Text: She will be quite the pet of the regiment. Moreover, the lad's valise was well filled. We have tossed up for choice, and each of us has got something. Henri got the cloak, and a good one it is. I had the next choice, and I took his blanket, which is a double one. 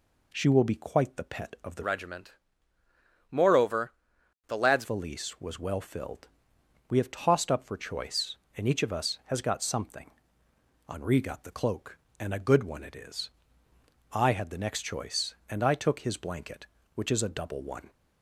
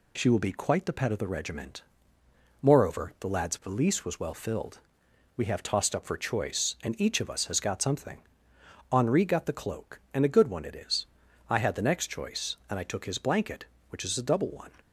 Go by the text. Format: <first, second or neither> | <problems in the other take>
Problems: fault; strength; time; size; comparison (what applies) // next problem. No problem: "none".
second | changes voice from "regiment" to "lad's"; from 1.8 to 4.8 s; 3.0 s long